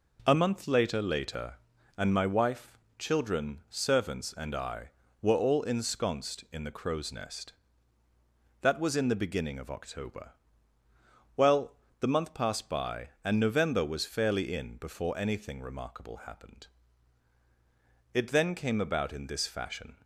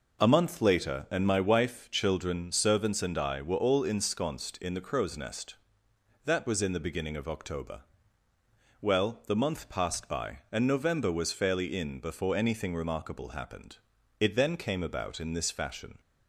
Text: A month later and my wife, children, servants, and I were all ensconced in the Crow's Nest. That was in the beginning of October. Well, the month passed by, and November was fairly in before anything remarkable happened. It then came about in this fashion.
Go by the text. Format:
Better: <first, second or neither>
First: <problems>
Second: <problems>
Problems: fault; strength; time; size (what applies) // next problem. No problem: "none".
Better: second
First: says "later" twice; at 1.0 s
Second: none